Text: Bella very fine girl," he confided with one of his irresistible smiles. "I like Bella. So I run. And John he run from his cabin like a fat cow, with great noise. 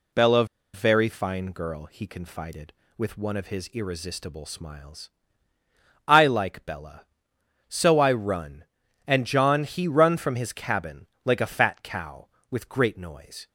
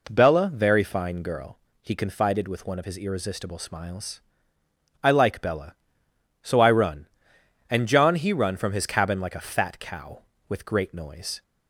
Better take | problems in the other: second | pauses between "Bella" and "very"; slight; at 0.4 s; 0.28 s long // pauses between "cabin" and "like"; slight; at 11.0 s; 0.18 s long

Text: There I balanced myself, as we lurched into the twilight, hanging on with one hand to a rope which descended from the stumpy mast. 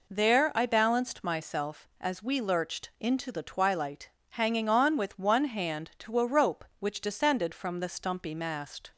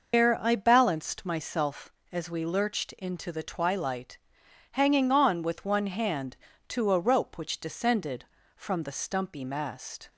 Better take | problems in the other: first | loses the start of "There"; at 0.1 s; 160 ms

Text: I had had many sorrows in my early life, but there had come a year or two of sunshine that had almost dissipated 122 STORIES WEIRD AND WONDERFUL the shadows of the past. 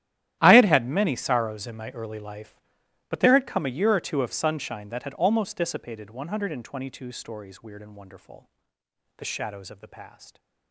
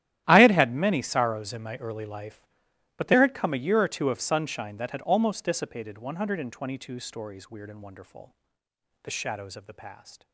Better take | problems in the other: neither | starts louder than the rest; strong; the same in both // pauses between "WONDERFUL" and "the"; noticeable; the same in both

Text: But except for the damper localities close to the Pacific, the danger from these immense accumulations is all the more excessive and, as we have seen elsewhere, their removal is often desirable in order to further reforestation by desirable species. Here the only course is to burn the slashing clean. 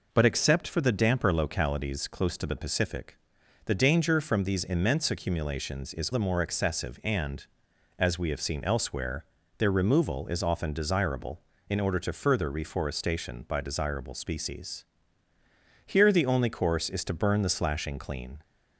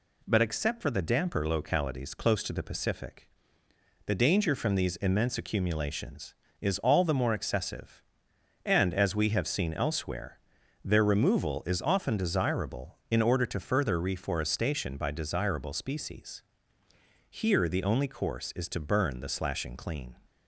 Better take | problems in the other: second | skips "all"; at 6.1 s

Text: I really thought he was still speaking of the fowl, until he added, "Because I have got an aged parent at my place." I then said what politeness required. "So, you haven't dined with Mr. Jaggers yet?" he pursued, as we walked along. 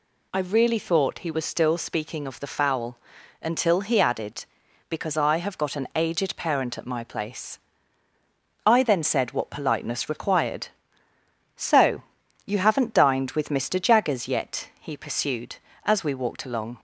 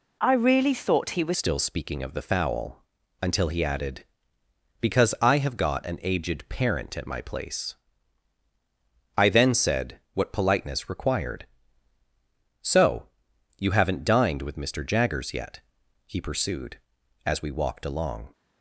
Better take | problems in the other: first | changes voice at "still"; from 1.3 s on; 17.0 s long // pauses between "said" and "what"; slight; at 9.9 s; 0.16 s long

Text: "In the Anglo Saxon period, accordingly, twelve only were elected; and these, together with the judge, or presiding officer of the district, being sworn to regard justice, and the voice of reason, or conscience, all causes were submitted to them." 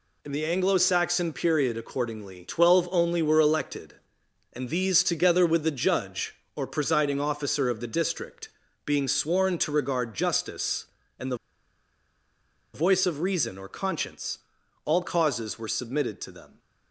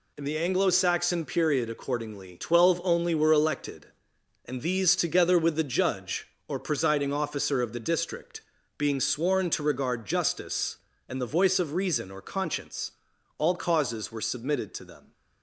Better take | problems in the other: second | pauses between "the" and "voice"; strong; at 11.3 s; 1.3 s long

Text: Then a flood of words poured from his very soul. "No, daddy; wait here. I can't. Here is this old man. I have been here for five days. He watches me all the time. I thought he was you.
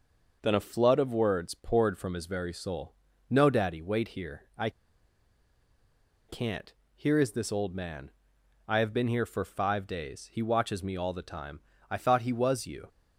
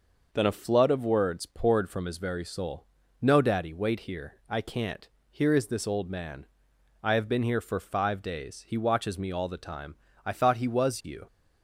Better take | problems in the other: second | pauses between "I" and "can't"; strong; at 4.6 s; 1.5 s long

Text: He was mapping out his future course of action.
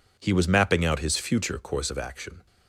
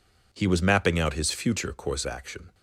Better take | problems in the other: first | skips "of"; at 2.0 s

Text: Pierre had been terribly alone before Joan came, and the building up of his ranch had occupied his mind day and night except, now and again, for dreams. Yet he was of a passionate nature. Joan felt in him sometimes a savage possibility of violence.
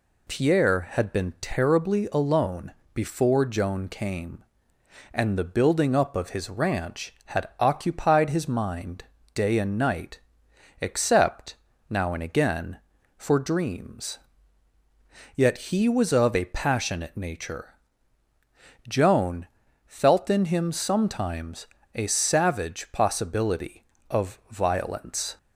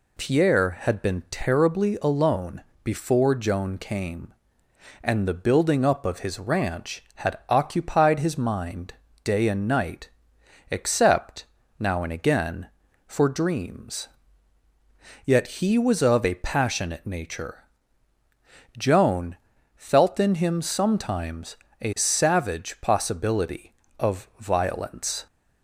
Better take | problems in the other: neither | pauses between "alone" and "before"; slight; the same in both // pauses between "mind" and "day"; slight; the same in both // pauses between "night" and "except"; noticeable; the same in both // pauses between "Joan" and "felt"; the same in both // pauses between "sometimes" and "a"; slight; the same in both

